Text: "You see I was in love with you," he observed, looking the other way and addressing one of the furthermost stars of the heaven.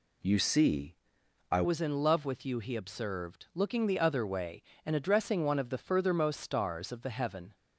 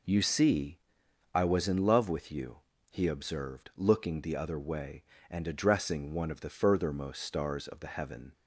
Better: second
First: pauses between "see" and "I"; noticeable; at 0.9 s; 0.54 s long // changes voice at "was"; from 1.6 s on; 5.9 s long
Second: pauses between "see" and "I"; noticeable; at 0.7 s; 0.54 s long

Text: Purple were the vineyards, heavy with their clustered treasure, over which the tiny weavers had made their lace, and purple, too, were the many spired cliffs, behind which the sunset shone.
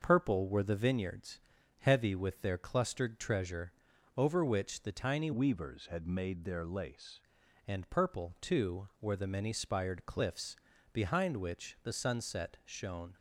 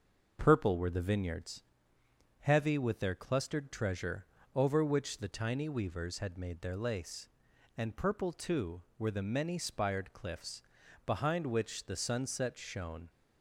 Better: second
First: starts louder than the rest; until 1.0 s; 6.5 dB // changes voice from "weavers" to "lace"; from 5.3 to 7.2 s; 1.9 s long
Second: starts louder than the rest; noticeable; until 1.4 s; 6 dB

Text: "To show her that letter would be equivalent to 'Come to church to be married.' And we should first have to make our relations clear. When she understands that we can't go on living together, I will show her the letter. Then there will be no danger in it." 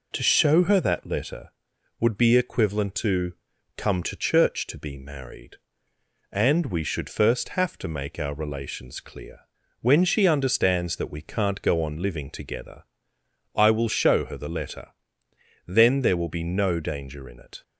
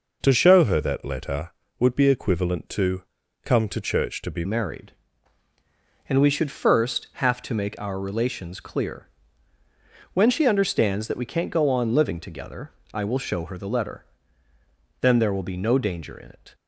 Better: first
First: pauses between "to" and "Come"; at 3.3 s; 0.42 s long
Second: pauses between "to" and "Come"; at 3.0 s; 0.38 s long // changes voice at "married"; from 4.4 s on; 12.1 s long

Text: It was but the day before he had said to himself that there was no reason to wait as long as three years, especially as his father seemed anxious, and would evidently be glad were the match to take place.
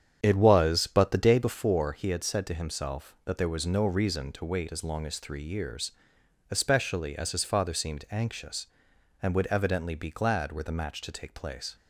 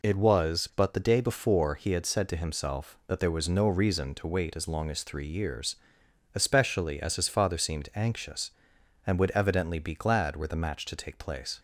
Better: second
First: starts louder than the rest; strong; until 1.6 s; 8 dB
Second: none

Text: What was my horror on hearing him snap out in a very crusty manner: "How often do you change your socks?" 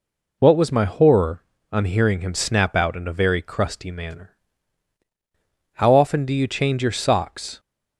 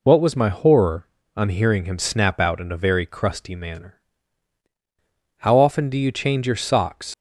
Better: first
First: none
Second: leaves "socks" unfinished; at 7.1 s; 100 ms

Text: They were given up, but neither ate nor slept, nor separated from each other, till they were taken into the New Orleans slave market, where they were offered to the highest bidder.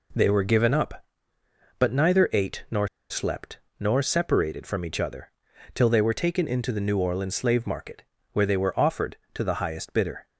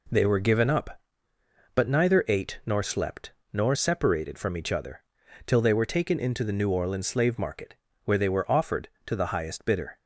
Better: second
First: pauses between "nor" and "slept"; slight; at 2.8 s; 0.23 s long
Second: none

